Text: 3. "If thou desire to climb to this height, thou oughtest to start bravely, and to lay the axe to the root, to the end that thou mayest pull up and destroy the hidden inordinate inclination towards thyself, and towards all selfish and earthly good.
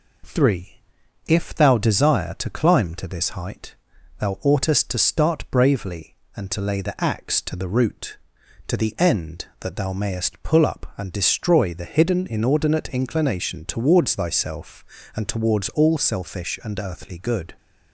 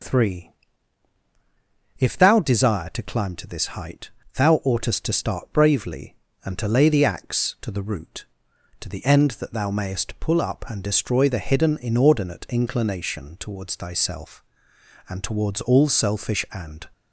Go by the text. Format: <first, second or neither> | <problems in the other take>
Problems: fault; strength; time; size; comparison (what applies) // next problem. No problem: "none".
first | stops before "earthly good"; at 16.9 s